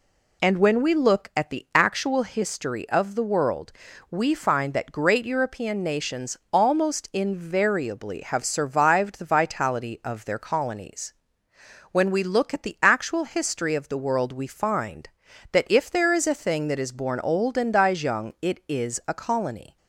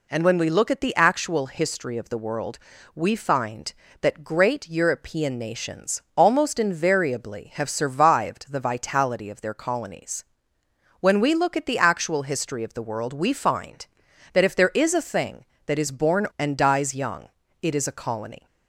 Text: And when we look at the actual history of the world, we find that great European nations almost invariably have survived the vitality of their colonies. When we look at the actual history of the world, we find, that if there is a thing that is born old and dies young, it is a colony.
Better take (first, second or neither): first